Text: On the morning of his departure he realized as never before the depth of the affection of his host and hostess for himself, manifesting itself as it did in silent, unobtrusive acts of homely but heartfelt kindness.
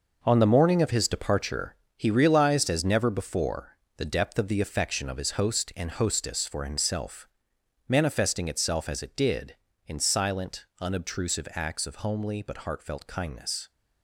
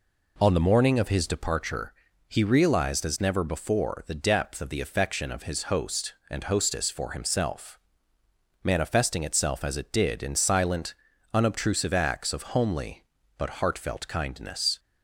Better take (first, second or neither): second